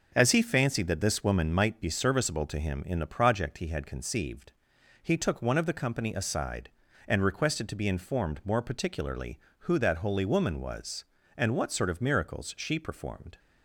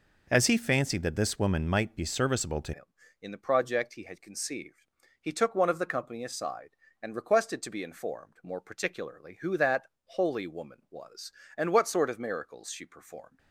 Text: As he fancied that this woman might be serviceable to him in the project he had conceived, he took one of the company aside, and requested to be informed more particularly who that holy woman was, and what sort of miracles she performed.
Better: first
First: none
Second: changes voice at "him"; from 2.7 s on; 10.6 s long // pauses between "that" and "holy"; slight; at 9.8 s; 0.16 s long

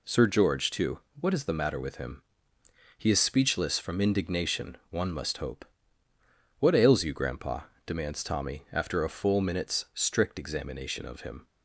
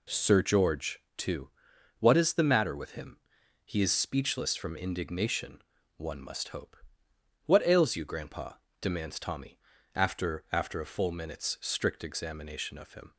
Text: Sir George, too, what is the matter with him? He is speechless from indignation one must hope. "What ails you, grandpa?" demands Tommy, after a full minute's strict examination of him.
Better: first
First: none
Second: pauses between "indignation" and "one"; slight; at 5.6 s; 0.34 s long // says "after" twice; at 10.5 s

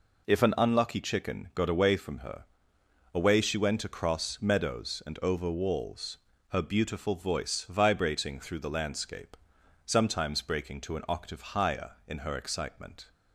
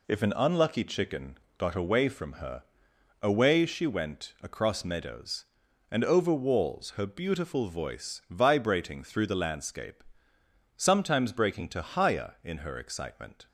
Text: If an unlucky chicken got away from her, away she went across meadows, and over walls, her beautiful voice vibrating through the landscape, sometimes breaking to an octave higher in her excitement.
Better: first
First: none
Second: pauses between "chicken" and "got"; slight; at 1.3 s; 0.18 s long // skips "an octave"; at 11.8 s

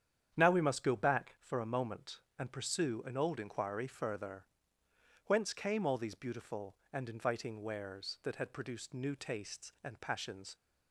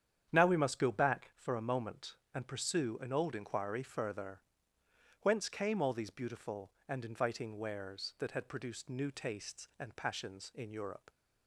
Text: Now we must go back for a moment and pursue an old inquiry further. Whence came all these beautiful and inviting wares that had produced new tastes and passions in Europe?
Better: second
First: starts louder than the rest; strong; until 1.3 s; 9 dB // stops before "in Europe"; at 10.5 s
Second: starts louder than the rest; strong; until 1.3 s; 9 dB

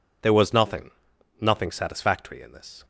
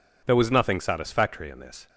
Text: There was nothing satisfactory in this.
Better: second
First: says "nothing" twice; at 1.3 s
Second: none

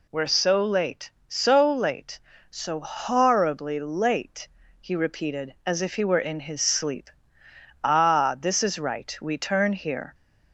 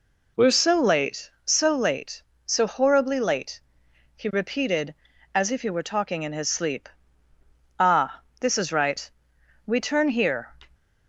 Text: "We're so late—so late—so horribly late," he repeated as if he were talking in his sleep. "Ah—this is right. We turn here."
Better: second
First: skips "talking"; at 6.1 s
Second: none

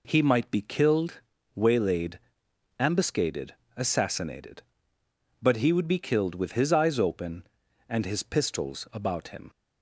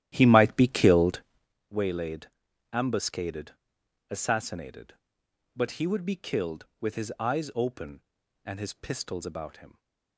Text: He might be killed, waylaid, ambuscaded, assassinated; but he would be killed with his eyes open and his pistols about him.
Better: first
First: none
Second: starts louder than the rest; strong; until 1.5 s; 12.5 dB

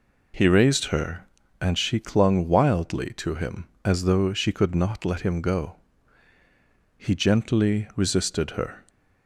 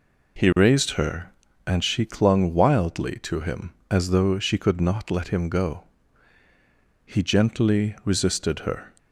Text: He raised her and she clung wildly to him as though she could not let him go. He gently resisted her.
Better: neither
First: none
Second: none

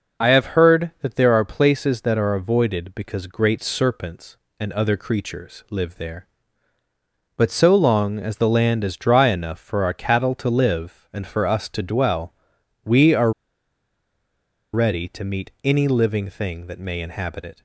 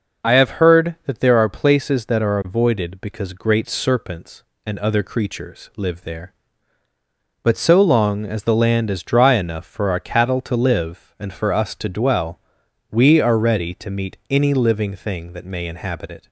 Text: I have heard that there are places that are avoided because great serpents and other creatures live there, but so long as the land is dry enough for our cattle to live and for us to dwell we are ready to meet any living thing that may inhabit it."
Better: second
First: pauses between "dwell" and "we"; noticeable; at 12.3 s; 0.54 s long // pauses between "are" and "ready"; strong; at 13.3 s; 1.4 s long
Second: pauses between "dwell" and "we"; noticeable; at 12.3 s; 0.54 s long

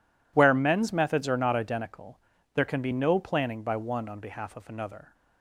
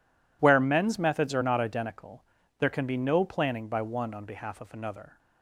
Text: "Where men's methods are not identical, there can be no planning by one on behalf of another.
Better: neither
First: none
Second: none

